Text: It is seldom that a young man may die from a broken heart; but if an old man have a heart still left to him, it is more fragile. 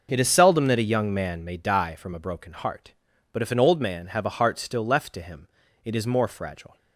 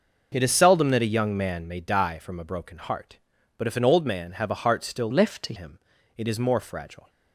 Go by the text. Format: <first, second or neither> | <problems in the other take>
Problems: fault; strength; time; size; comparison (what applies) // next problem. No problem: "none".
first | changes voice from "left" to "to"; from 5.1 to 5.5 s; 0.4 s long